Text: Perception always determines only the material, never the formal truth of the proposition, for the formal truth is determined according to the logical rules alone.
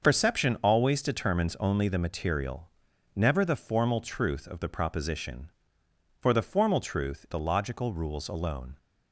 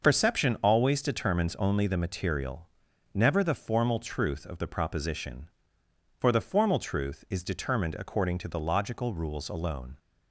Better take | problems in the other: second | starts louder than the rest; until 1.0 s; 6.5 dB; also in the second // skips "is determined according to"; at 7.2 s

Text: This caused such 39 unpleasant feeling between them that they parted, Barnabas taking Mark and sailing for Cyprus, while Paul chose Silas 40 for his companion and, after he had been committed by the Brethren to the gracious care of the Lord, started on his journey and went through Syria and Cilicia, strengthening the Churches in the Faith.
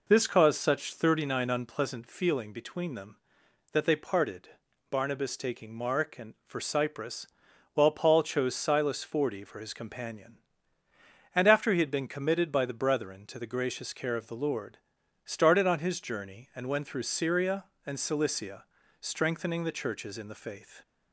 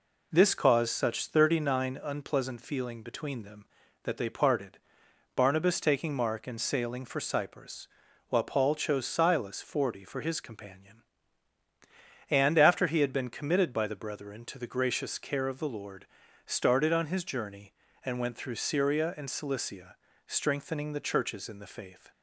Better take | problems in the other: second | skips "sailing"; at 6.4 s

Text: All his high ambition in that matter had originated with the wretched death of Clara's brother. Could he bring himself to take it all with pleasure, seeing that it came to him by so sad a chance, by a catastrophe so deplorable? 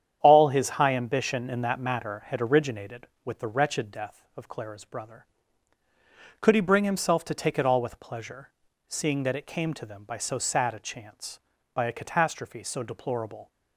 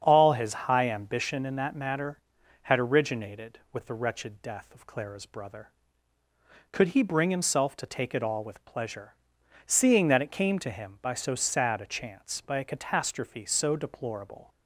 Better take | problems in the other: second | starts louder than the rest; strong; until 1.2 s; 9 dB; strong in the second // says "them" for "him"; at 9.8 s

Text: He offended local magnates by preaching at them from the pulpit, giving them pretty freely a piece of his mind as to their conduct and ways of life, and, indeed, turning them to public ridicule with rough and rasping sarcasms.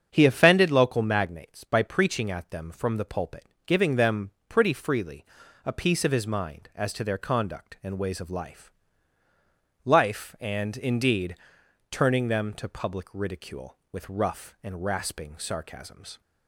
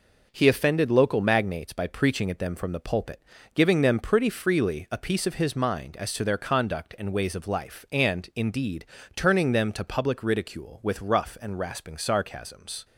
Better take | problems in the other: second | starts louder than the rest; strong; until 1.1 s; 7.5 dB // pauses between "them" and "pretty"; slight; at 4.3 s; 0.18 s long // pauses between "freely" and "a"; at 5.2 s; 0.40 s long // says "life" twice; at 9.8 s

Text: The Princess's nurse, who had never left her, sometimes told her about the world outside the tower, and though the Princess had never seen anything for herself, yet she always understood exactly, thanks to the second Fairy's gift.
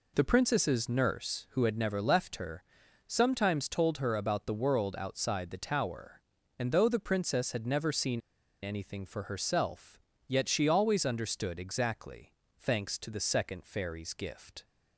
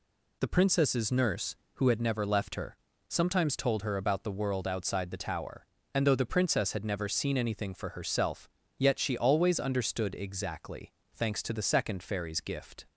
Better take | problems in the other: second | pauses between "seen" and "anything"; at 8.2 s; 0.42 s long

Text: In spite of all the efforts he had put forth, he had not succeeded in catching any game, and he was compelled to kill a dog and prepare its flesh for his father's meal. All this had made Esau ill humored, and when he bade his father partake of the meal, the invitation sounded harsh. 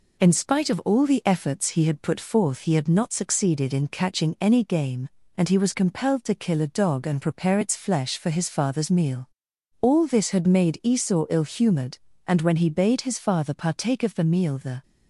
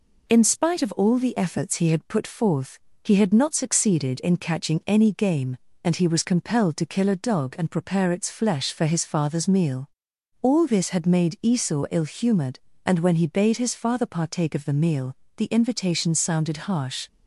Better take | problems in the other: second | stops before "invitation sounded harsh"; at 14.8 s

